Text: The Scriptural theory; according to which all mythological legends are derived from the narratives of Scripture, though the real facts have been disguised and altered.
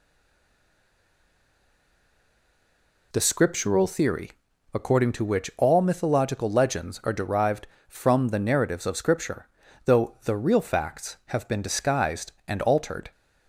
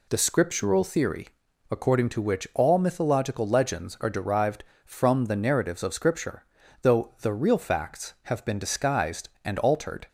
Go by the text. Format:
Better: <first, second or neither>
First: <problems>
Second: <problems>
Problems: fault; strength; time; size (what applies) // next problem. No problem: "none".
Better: second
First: stays silent before the first word; strong; until 3.1 s; 3.1 s long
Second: none